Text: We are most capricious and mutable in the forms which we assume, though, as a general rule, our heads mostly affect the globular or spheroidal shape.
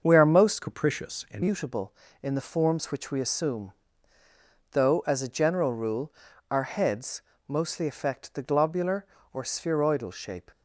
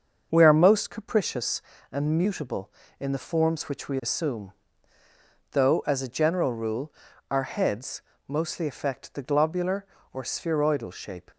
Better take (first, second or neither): second